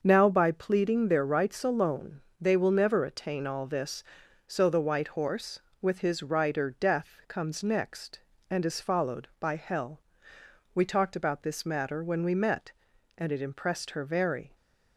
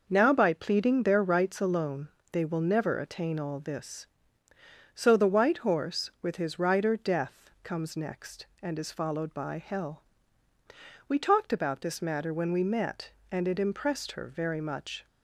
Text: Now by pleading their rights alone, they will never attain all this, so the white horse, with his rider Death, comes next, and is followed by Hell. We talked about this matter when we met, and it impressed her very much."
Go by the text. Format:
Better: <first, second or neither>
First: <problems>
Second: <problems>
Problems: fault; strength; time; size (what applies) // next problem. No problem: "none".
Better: second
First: starts louder than the rest; until 1.0 s; 6.5 dB // stops before "much"; at 14.5 s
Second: none